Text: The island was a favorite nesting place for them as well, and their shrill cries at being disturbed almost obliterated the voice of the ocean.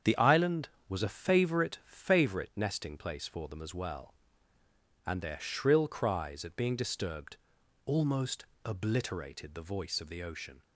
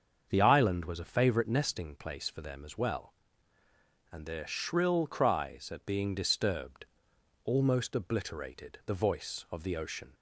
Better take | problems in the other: second | starts louder than the rest; strong; until 1.2 s; 8 dB; also in the second // says "favorite" twice; at 1.8 s // pauses between "disturbed" and "almost"; noticeable; at 7.3 s; 0.48 s long; noticeable in the second // pauses between "almost" and "obliterated"; slight; at 8.4 s; 0.18 s long

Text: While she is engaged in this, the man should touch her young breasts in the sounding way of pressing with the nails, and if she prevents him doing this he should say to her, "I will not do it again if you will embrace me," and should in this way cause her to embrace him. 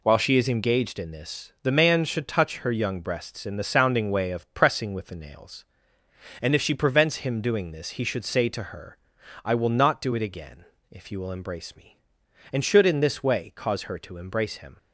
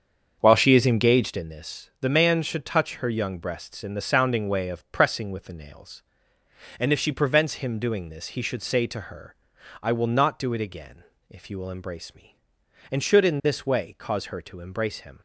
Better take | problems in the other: first | starts louder than the rest; until 1.5 s; 7 dB // pauses between "again" and "if"; slight; at 11.0 s; 0.26 s long; slight in the first

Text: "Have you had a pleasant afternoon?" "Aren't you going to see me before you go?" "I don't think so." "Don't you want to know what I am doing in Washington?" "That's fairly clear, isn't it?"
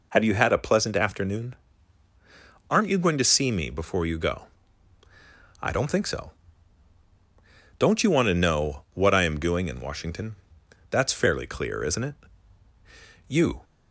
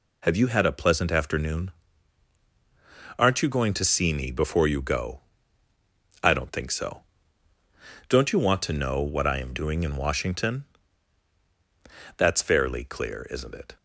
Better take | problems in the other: second | goes on to say "You"; slight; from 13.2 s on; 0.36 s long

